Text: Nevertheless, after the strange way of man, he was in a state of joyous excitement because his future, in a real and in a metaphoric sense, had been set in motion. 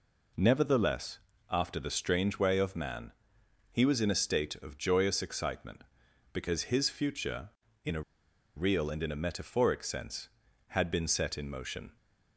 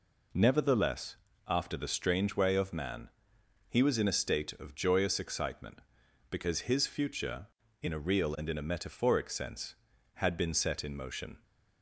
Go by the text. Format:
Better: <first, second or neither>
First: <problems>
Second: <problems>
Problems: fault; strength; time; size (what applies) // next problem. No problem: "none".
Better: second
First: pauses between "a" and "real"; noticeable; at 8.0 s; 0.54 s long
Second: none